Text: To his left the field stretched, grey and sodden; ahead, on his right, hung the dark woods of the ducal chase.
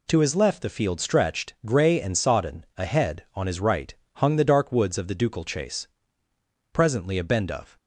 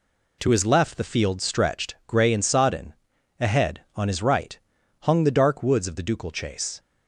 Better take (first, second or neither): second